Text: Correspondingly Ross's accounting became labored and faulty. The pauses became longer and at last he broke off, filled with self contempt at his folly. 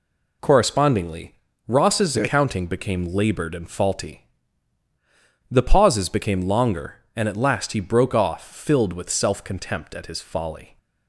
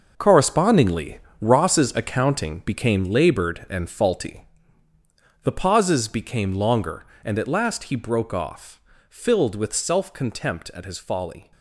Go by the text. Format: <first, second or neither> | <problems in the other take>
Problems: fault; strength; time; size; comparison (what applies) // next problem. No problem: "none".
first | gets quieter; strong; throughout; 11 dB // pauses between "Correspondingly" and "Ross's"; slight; at 1.1 s; 0.22 s long; slight in the first